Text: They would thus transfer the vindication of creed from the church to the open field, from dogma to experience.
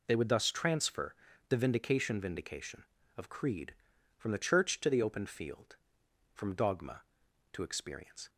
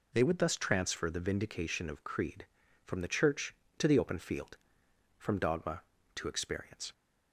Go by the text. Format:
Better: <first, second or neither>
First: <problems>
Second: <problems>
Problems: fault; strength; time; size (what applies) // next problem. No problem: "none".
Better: second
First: pauses between "transfer" and "the"; slight; at 1.1 s; 0.34 s long // says "vindication" twice; at 2.2 s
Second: none